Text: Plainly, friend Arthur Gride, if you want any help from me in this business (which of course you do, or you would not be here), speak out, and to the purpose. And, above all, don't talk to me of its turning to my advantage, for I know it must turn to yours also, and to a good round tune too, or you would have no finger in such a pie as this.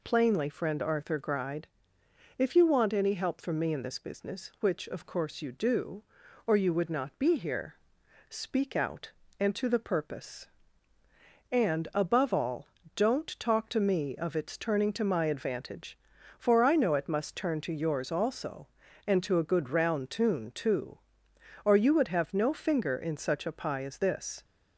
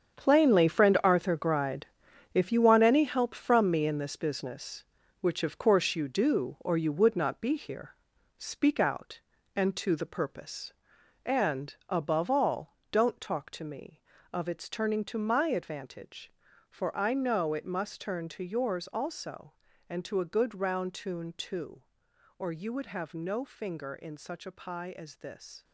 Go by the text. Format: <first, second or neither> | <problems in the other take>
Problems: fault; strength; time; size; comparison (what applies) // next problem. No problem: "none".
first | gets quieter; strong; throughout; 11 dB